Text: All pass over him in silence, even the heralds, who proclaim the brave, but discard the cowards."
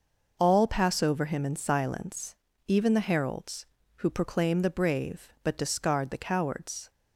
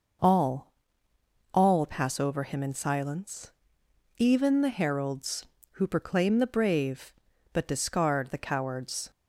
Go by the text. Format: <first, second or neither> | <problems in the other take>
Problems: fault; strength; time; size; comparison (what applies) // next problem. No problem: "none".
first | says "All" twice; at 1.5 s